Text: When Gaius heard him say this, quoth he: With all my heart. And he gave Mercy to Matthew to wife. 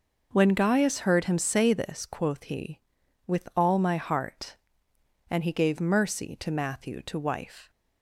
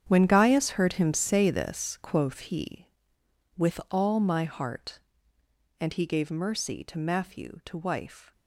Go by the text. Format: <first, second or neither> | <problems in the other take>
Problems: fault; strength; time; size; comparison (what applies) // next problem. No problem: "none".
first | gets quieter; strong; throughout; 13 dB